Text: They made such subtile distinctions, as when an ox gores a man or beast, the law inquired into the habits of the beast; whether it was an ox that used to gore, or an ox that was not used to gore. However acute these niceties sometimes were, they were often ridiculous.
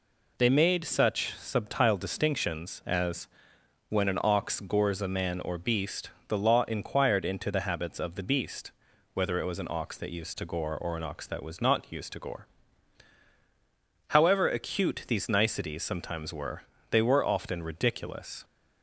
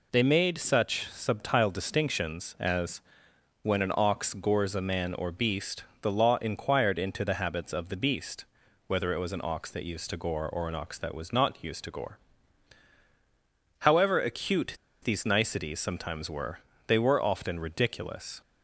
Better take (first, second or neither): first